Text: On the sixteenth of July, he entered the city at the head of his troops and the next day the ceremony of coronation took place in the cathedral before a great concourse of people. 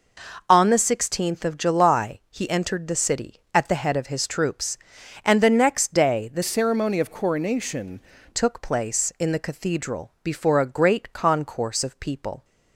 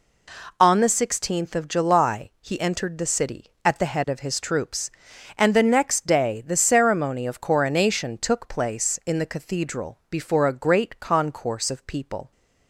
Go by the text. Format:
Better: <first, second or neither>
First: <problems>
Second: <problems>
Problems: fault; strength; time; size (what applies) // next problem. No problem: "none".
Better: second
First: changes voice from "ceremony" to "coronation"; from 6.4 to 7.9 s; 1.5 s long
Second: none